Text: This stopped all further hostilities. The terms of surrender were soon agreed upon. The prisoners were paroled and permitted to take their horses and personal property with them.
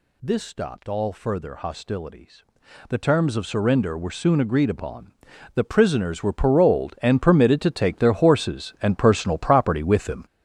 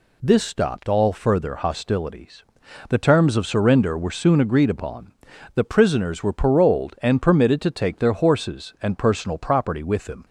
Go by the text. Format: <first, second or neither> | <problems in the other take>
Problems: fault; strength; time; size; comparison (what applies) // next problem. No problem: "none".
second | gets louder; strong; throughout; 9 dB